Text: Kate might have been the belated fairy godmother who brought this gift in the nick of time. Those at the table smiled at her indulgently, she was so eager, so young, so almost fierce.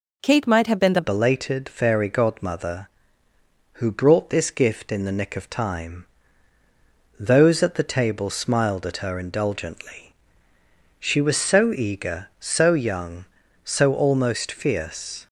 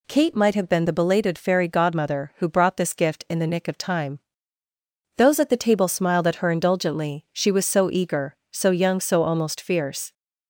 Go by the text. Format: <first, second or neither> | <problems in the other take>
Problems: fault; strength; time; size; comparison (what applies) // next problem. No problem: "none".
second | changes voice at "belated"; from 1.0 s on; 14.2 s long